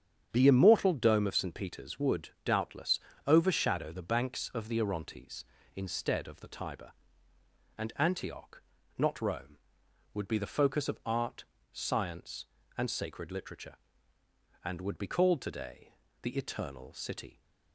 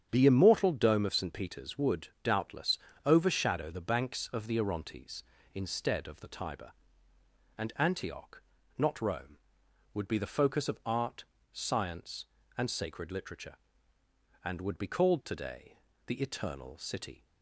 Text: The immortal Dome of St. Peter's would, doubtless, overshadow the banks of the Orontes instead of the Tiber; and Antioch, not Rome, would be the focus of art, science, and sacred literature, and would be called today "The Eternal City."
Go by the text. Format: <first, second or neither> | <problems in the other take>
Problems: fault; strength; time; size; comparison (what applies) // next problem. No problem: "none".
neither | starts louder than the rest; strong; the same in both // pauses between "today" and "The"; slight; the same in both